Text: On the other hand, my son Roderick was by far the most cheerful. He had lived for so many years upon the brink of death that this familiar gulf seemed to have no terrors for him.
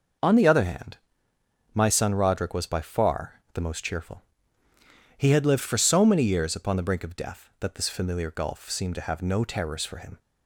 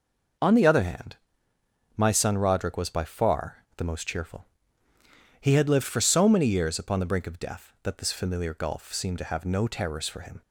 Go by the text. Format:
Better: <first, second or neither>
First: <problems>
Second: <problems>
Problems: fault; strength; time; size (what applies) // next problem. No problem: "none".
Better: neither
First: none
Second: none